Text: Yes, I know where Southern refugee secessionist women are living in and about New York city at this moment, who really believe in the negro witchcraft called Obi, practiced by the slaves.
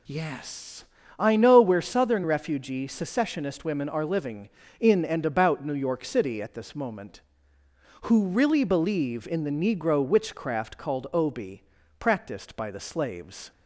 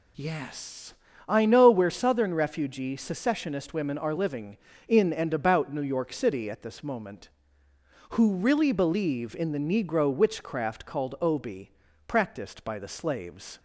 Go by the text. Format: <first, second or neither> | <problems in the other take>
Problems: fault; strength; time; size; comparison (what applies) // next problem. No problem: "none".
neither | none